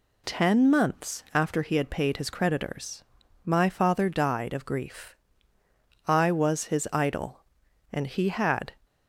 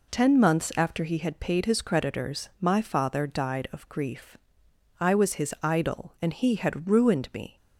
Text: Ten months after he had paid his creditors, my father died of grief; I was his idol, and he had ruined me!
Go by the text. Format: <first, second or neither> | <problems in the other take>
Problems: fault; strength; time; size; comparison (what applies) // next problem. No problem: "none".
second | stops before "ruined me"; at 8.8 s